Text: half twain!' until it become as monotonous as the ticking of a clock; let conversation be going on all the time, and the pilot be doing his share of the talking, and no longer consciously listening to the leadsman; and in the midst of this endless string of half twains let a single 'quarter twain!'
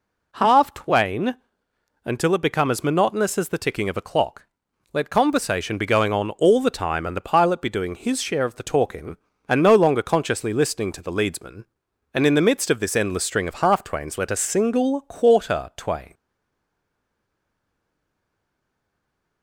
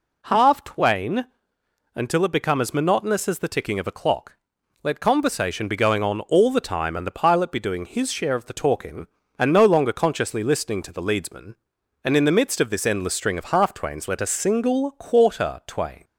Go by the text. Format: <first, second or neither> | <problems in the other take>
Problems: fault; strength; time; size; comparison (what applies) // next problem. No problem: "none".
second | stays silent after the last word; strong; from 16.1 s on; 3.3 s long